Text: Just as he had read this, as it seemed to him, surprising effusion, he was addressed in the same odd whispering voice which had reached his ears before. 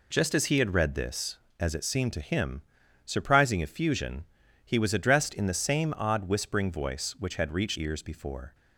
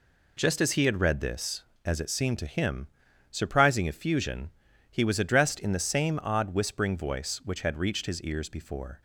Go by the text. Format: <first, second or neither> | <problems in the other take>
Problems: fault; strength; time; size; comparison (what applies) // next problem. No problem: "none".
second | skips "his"; at 7.7 s